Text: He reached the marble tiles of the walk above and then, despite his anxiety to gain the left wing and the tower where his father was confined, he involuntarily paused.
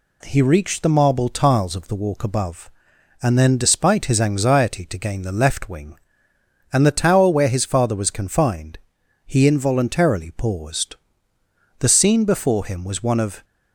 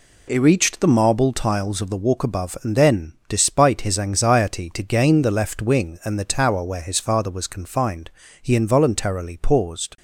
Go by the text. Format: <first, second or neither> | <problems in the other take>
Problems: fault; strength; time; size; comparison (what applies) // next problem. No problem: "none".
second | goes on to say "The scene before him was one of"; from 11.7 s on; 1.6 s long